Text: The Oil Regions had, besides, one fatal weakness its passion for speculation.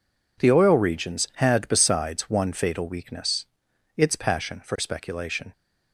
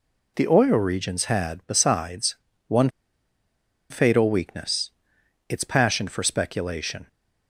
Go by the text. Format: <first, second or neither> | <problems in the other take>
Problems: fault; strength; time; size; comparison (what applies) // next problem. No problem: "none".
first | pauses between "one" and "fatal"; at 2.8 s; 1.0 s long // pauses between "weakness" and "its"; noticeable; at 4.9 s; 0.58 s long; noticeable in the first